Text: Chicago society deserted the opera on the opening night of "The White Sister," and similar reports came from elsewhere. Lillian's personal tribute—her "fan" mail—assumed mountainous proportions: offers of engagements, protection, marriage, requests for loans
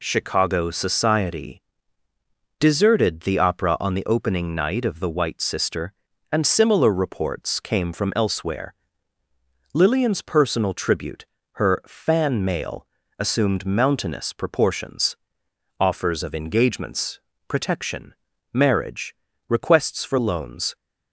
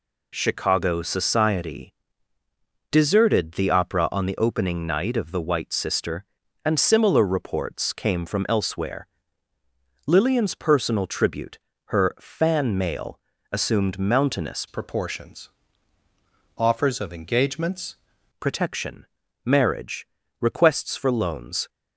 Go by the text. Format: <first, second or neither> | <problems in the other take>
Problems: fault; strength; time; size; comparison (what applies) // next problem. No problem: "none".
first | pauses between "society" and "deserted"; noticeable; at 1.9 s; 0.96 s long; noticeable in the first // changes voice from "proportions" to "engagements"; from 14.6 to 17.9 s; 3.3 s long